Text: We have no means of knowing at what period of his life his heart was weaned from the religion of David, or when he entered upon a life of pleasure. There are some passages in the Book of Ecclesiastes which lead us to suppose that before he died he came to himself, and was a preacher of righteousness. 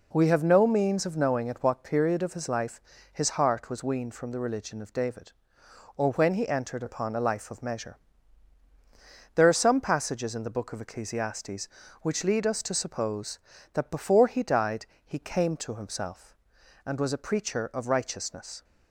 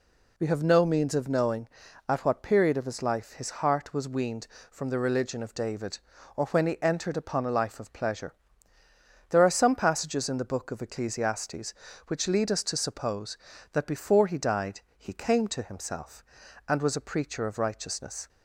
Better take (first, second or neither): second